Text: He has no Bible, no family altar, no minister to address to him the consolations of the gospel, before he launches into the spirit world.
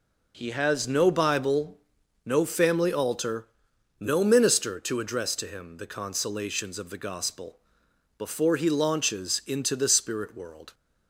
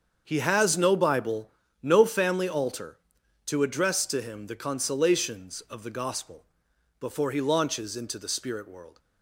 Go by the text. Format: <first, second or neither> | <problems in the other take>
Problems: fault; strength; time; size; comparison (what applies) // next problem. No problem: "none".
first | starts louder than the rest; until 1.2 s; 7 dB // skips "no minister"; at 3.2 s